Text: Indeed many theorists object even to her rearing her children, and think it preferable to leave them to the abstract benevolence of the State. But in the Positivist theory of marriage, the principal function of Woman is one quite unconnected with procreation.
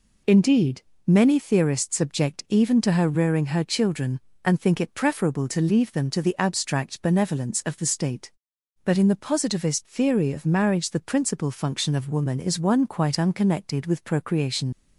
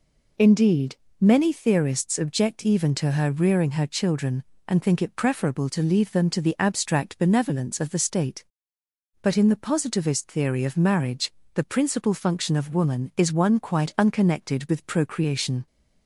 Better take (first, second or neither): second